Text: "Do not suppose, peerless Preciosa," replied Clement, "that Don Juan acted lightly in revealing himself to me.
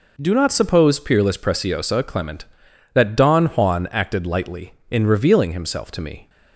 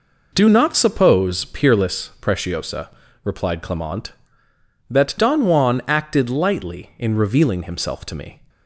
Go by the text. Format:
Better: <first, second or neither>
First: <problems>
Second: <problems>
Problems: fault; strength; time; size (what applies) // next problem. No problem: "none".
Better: second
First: skips "replied"; at 2.0 s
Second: none